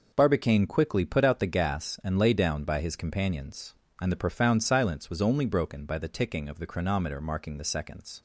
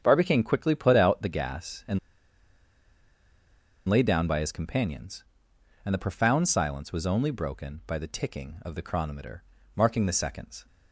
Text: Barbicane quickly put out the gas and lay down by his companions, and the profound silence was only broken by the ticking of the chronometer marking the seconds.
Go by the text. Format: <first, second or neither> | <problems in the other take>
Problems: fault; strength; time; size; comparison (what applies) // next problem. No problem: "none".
first | starts louder than the rest; strong; until 1.0 s; 8 dB // pauses between "and" and "lay"; strong; at 1.9 s; 1.8 s long // pauses between "chronometer" and "marking"; slight; at 9.4 s; 0.32 s long